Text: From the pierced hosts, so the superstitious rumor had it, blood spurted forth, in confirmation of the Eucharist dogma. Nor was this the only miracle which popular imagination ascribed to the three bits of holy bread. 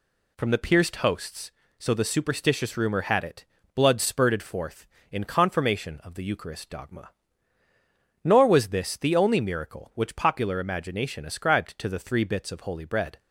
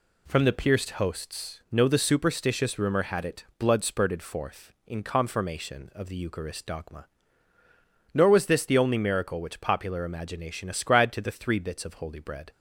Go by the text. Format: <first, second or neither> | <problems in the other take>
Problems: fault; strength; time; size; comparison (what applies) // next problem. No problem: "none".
first | says "no" for "so"; at 1.7 s